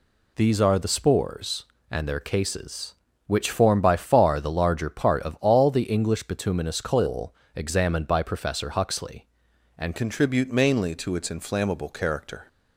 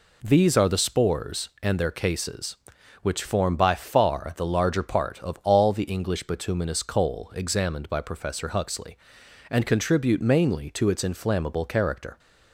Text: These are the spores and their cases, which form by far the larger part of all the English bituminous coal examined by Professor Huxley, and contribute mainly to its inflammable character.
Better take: second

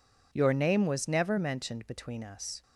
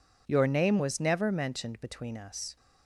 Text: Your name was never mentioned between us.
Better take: neither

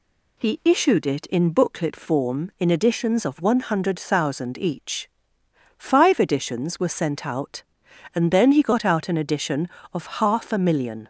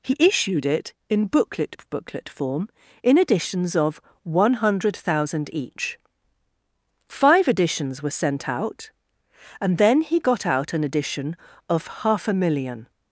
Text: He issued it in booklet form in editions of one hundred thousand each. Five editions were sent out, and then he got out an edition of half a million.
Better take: first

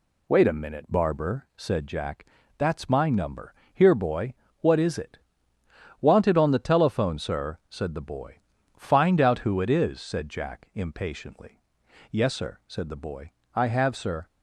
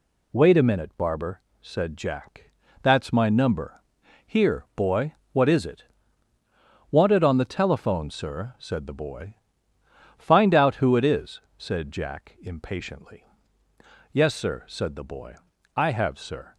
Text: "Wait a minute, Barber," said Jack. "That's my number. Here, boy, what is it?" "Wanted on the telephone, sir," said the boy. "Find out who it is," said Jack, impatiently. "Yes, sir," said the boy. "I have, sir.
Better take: neither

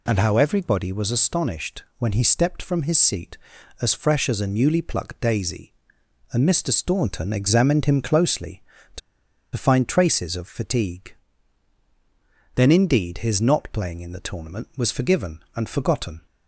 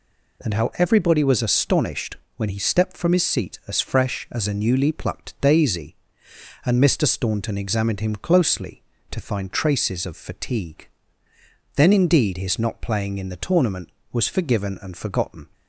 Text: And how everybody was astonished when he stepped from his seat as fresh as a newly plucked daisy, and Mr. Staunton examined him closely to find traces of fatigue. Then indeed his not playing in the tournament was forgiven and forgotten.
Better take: second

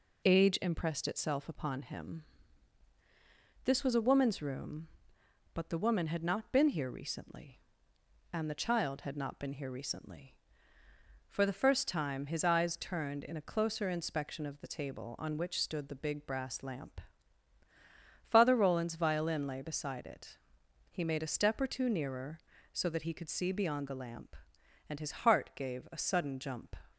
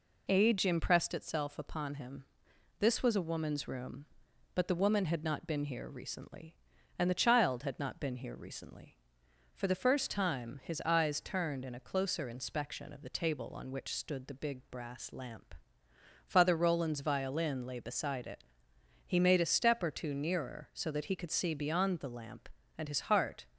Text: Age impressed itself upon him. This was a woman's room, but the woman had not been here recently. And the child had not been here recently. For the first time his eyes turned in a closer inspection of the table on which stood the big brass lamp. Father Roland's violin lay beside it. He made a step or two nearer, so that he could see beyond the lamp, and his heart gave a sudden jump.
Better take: first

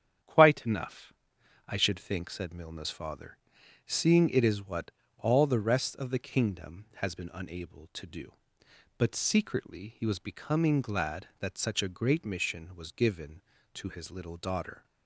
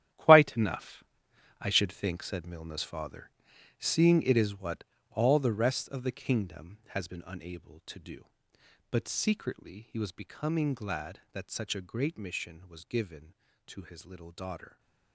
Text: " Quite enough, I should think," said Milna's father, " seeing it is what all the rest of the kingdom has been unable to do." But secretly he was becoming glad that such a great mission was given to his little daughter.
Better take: first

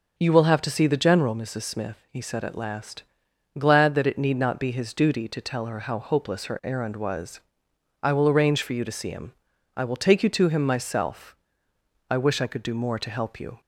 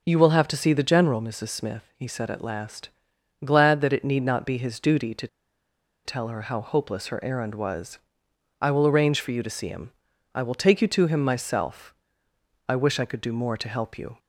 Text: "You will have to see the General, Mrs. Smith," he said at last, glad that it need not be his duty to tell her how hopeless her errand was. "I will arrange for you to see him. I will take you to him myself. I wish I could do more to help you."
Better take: first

